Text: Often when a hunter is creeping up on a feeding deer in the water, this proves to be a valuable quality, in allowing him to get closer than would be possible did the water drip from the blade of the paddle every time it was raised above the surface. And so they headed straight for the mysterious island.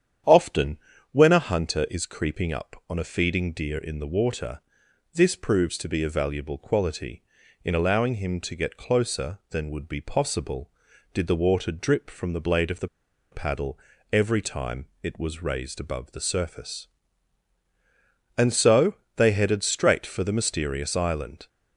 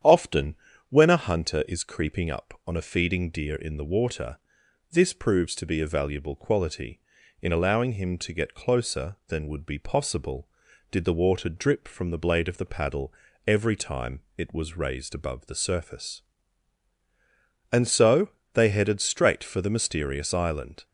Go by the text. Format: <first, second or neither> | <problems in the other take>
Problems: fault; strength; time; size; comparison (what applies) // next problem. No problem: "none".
second | starts louder than the rest; strong; until 1.5 s; 9 dB; strong in the second // pauses between "Often" and "when"; slight; at 0.7 s; 0.32 s long; slight in the second // pauses between "the" and "paddle"; at 12.8 s; 0.44 s long // pauses between "paddle" and "every"; slight; at 13.7 s; 0.34 s long; slight in the second // pauses between "time" and "it"; slight; at 14.8 s; 0.16 s long; slight in the second // pauses between "so" and "they"; slight; at 18.9 s; 0.22 s long; slight in the second